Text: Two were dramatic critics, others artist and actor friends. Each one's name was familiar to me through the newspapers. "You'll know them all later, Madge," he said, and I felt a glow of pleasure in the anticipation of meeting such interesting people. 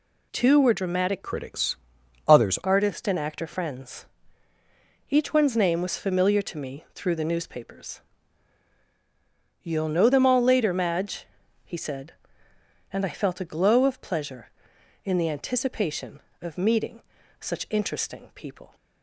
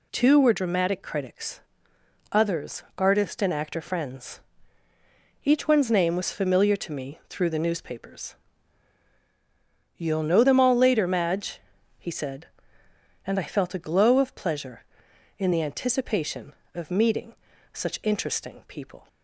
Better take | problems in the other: second | changes voice from "critics" to "others"; from 1.2 to 2.5 s; 1.3 s long // pauses between "meeting" and "such"; at 17.0 s; 0.40 s long; also in the second

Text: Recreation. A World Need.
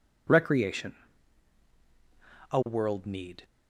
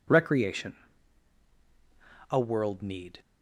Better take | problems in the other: neither | none

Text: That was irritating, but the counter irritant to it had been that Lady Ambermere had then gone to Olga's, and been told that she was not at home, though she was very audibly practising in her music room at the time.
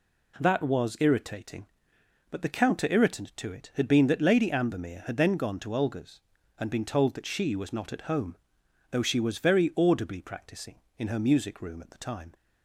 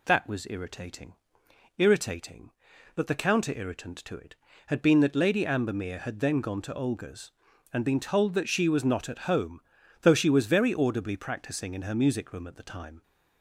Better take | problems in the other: first | says "irritating" twice; at 1.7 s

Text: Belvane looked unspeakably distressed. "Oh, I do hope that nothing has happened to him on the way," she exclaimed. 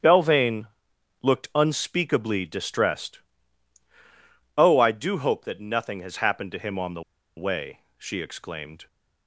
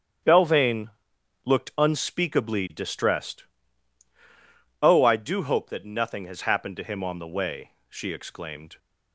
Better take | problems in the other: second | starts louder than the rest; strong; until 1.5 s; 9 dB; strong in the second // pauses between "Belvane" and "looked"; noticeable; at 0.6 s; 0.56 s long; noticeable in the second // pauses between "the" and "way"; slight; at 7.0 s; 0.33 s long

